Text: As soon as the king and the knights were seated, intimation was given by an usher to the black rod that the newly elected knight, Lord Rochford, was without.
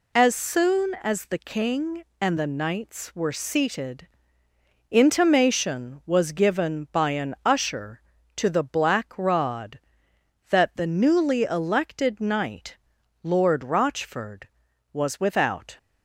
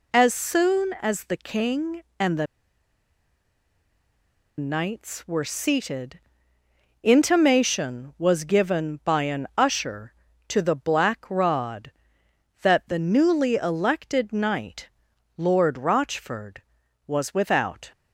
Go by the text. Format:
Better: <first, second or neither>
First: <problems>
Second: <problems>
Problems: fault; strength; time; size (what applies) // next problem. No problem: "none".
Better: first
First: none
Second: pauses between "the" and "knights"; strong; at 2.4 s; 2.1 s long